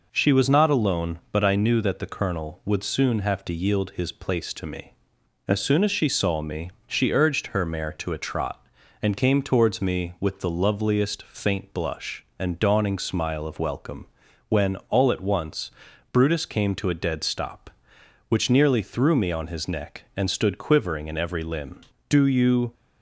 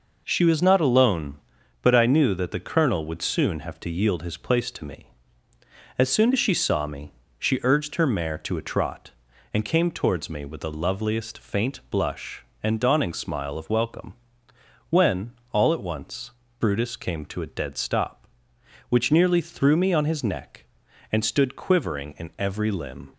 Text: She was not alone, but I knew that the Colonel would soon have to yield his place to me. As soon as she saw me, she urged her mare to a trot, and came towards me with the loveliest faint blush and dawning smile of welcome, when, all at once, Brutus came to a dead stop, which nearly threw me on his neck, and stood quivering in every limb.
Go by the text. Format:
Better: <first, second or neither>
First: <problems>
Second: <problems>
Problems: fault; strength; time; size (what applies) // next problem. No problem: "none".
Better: second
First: goes on to say "Do you"; noticeable; from 22.0 s on; 0.64 s long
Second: none